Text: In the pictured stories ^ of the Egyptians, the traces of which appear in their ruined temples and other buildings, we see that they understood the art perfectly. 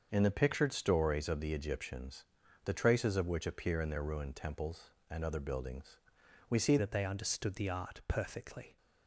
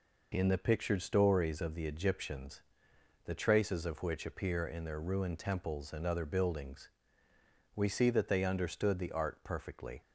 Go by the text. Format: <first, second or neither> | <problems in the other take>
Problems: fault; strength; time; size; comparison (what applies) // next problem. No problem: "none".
second | starts louder than the rest; until 1.1 s; 6.5 dB // changes voice at "that"; from 6.7 s on; 2.0 s long